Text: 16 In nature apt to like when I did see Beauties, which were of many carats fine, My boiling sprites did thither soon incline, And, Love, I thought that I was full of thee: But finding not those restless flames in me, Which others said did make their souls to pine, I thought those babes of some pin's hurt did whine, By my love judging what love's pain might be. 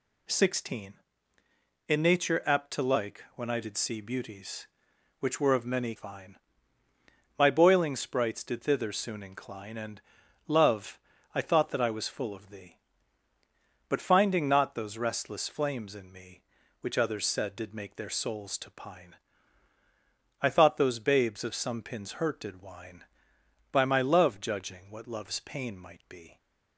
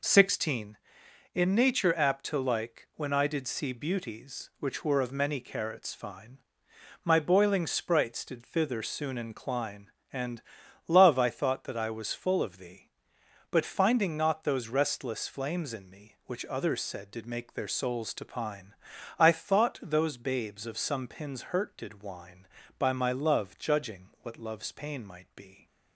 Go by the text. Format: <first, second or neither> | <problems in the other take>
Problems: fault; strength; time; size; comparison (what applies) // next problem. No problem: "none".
second | skips "carats"; at 5.9 s